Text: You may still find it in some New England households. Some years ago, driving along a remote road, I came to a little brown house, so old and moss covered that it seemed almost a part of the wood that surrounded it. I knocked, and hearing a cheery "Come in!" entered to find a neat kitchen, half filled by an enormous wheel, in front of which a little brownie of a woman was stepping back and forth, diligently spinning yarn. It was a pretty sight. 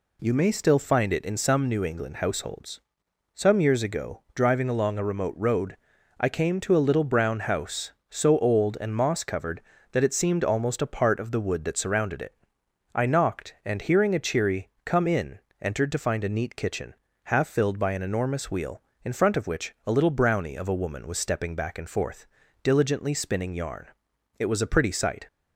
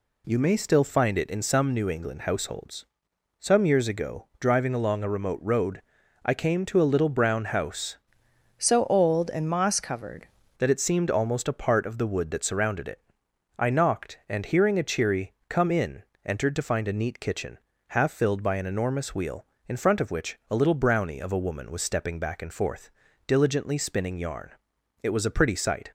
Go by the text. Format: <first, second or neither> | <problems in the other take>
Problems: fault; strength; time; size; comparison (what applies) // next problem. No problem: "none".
first | changes voice from "so" to "covered"; from 8.5 to 10.2 s; 1.7 s long // pauses between "cheery" and "Come"; slight; at 15.3 s; 0.16 s long; slight in the first